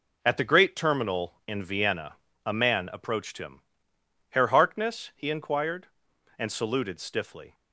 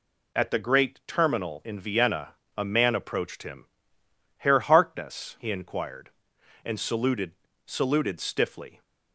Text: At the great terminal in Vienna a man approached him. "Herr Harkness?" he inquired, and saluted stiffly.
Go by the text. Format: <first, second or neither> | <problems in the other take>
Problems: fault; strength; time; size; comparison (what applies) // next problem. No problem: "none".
first | pauses between "Vienna" and "a"; slight; at 2.3 s; 0.24 s long; slight in the first // says "saluted" twice; at 7.6 s